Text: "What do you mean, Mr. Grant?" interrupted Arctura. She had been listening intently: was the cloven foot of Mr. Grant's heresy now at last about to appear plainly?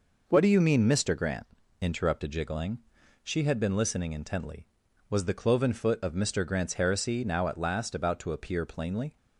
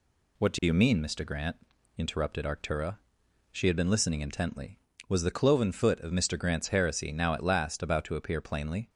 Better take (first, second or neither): second